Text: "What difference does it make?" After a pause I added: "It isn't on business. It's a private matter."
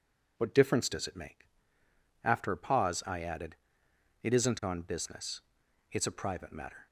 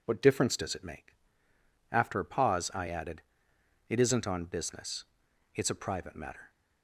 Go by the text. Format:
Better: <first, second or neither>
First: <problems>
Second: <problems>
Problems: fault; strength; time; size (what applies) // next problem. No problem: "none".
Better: neither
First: none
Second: none